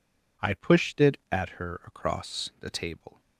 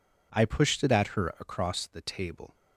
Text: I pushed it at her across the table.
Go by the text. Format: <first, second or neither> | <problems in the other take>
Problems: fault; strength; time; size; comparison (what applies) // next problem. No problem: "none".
neither | none